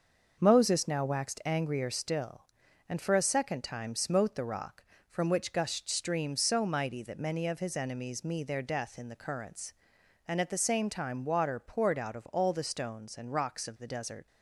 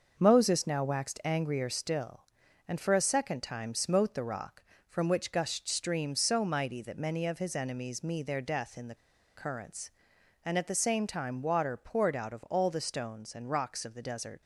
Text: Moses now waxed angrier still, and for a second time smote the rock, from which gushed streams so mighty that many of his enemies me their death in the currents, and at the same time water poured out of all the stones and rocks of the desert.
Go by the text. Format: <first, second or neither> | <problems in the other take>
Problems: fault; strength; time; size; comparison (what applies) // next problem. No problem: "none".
first | starts louder than the rest; until 1.1 s; 6 dB; also in the first // pauses between "the" and "currents"; at 8.9 s; 0.41 s long